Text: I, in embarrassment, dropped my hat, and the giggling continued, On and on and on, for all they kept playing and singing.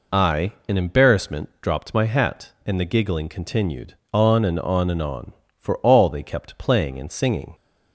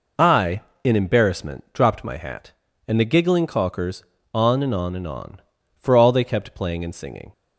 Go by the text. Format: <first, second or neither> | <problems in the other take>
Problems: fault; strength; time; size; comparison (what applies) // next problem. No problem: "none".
first | says "caulkers" for "continued"; at 3.4 s